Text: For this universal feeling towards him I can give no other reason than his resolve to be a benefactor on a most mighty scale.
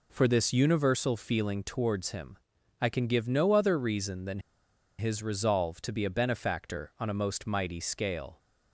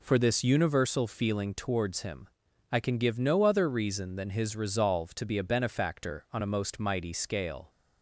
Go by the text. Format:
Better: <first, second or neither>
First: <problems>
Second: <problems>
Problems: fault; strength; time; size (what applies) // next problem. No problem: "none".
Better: second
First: pauses between "him" and "I"; at 2.3 s; 0.42 s long // pauses between "than" and "his"; noticeable; at 4.4 s; 0.58 s long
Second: pauses between "him" and "I"; at 2.2 s; 0.42 s long